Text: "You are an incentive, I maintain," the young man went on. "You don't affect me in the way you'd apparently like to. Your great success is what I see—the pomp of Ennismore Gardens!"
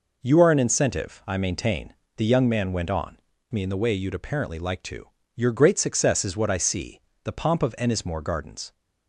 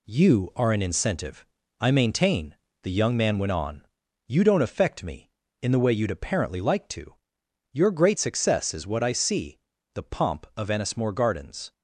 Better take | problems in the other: second | skips "You don't affect"; at 3.3 s

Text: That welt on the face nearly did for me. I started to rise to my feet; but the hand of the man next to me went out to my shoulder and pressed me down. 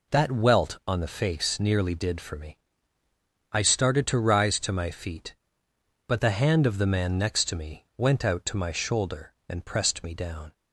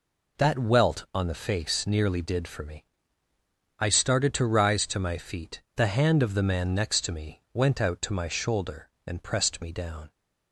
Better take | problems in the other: first | skips "but"; at 5.6 s

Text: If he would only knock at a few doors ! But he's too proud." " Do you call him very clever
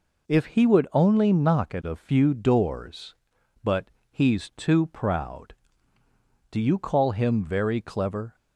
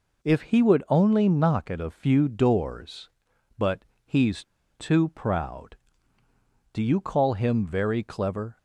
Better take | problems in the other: first | pauses between "But" and "he's"; slight; at 3.8 s; 0.24 s long; slight in the first // pauses between "he's" and "too"; slight; at 4.4 s; 0.35 s long

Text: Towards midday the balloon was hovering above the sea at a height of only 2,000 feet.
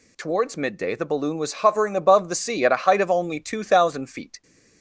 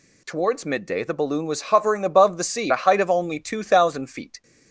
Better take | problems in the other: first | skips "at"; at 2.7 s

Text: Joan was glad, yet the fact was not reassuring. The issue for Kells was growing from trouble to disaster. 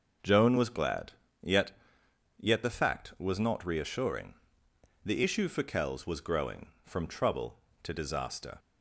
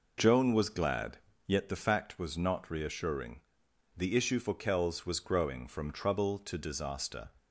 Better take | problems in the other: second | says "yet" twice; at 2.3 s

